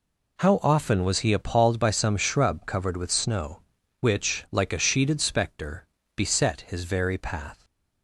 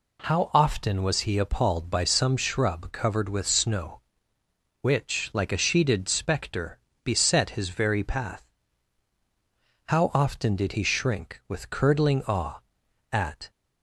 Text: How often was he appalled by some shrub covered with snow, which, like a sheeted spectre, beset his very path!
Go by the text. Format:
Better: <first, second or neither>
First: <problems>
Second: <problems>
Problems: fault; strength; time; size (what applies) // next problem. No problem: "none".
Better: first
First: none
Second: goes on to say "How often did he shrink with curdling awe at"; strong; from 9.8 s on; 3.6 s long